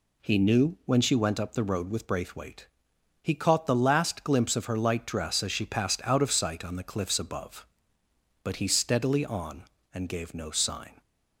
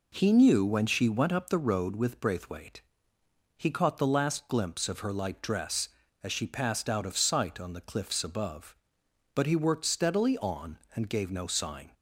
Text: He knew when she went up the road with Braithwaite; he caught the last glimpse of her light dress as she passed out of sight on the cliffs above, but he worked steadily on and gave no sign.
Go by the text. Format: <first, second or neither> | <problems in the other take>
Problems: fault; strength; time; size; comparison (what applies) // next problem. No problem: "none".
second | skips "worked"; at 8.6 s